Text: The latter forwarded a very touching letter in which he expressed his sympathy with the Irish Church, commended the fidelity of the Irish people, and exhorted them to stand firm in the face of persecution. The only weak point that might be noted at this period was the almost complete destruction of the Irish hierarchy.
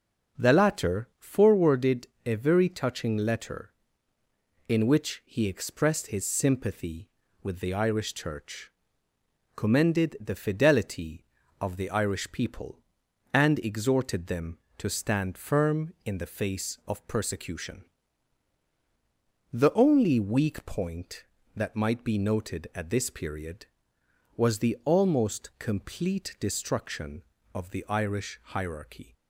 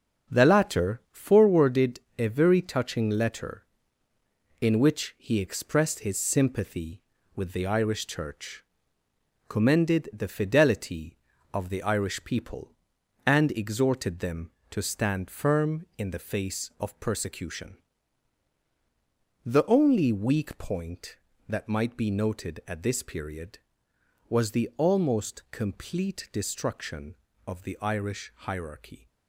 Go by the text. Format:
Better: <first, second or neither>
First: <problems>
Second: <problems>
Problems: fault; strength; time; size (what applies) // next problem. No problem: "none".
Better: first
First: pauses between "forwarded" and "a"; slight; at 2.0 s; 0.18 s long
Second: gets quieter; strong; throughout; 7 dB // pauses between "forwarded" and "a"; slight; at 1.9 s; 0.18 s long